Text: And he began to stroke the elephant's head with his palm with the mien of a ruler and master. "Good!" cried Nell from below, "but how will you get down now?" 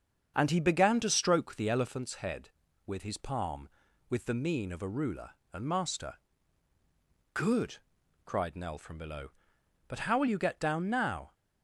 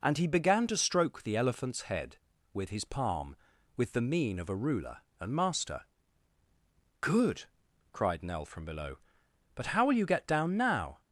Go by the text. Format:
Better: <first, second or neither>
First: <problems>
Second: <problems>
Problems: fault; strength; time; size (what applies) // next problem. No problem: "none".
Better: second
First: starts louder than the rest; strong; until 1.9 s; 7 dB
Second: none